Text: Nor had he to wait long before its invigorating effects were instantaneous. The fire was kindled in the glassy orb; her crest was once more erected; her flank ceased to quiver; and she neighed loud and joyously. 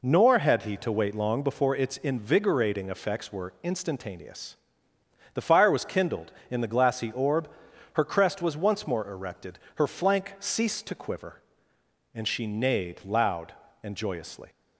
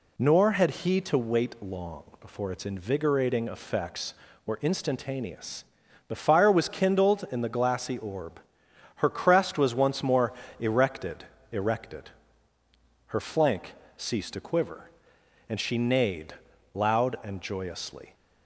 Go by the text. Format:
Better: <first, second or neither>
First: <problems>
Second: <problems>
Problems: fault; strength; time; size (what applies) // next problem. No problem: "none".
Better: first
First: none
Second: pauses between "long" and "before"; slight; at 2.0 s; 0.16 s long // pauses between "more" and "erected"; slight; at 10.3 s; 0.26 s long // says "erected" twice; at 11.5 s // pauses between "flank" and "ceased"; slight; at 13.7 s; 0.24 s long // pauses between "neighed" and "loud"; at 16.3 s; 0.40 s long